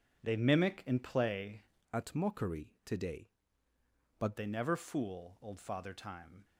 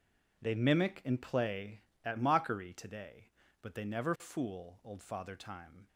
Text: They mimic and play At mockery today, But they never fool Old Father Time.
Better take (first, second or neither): second